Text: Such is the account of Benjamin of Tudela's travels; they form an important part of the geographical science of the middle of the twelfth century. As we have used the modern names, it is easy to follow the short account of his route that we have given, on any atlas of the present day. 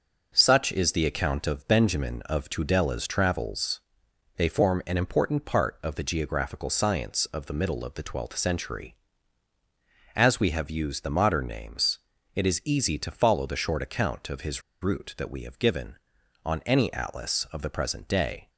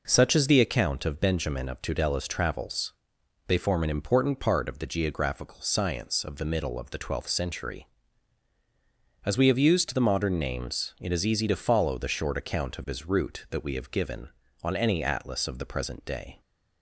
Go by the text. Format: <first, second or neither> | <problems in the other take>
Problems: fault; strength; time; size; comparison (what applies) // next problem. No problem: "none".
second | pauses between "his" and "route"; slight; at 14.6 s; 0.21 s long